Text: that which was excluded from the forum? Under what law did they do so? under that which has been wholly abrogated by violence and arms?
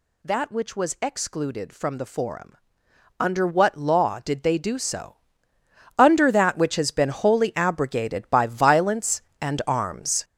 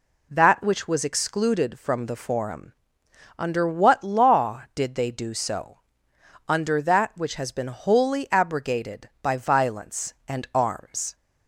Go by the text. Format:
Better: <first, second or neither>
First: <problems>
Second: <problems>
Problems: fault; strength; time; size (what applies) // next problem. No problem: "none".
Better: second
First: gets louder; strong; throughout; 9.5 dB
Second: none